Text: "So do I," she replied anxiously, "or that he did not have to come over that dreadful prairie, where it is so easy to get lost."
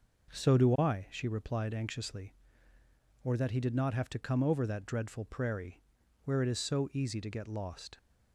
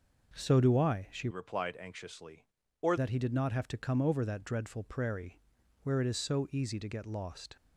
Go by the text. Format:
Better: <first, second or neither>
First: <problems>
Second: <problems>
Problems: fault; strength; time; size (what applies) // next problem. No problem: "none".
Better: first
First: none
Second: changes voice from "replied" to "or"; from 1.3 to 2.9 s; 1.6 s long